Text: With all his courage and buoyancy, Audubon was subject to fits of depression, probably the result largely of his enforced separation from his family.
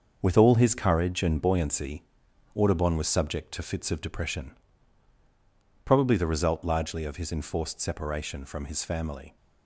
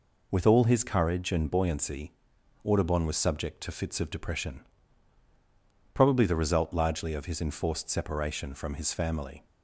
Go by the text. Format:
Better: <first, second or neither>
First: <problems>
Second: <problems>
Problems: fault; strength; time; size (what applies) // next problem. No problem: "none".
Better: second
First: gets quieter; strong; throughout; 8 dB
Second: none